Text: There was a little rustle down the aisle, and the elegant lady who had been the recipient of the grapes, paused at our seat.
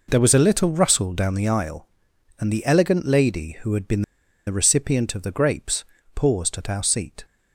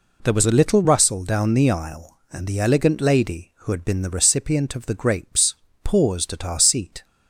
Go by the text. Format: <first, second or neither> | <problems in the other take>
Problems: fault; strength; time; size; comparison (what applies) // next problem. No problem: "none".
second | pauses between "been" and "the"; at 4.0 s; 0.45 s long